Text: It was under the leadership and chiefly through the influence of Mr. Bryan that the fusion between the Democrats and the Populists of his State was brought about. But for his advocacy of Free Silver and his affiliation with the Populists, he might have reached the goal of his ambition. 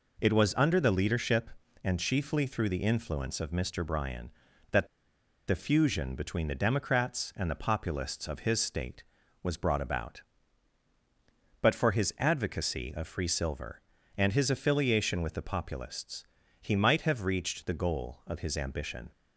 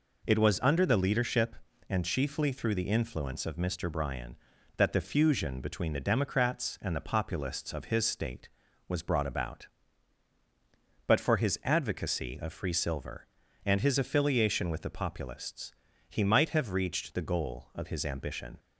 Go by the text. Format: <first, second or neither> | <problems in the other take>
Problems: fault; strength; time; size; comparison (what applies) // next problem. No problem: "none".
second | pauses between "that" and "the"; noticeable; at 4.8 s; 0.60 s long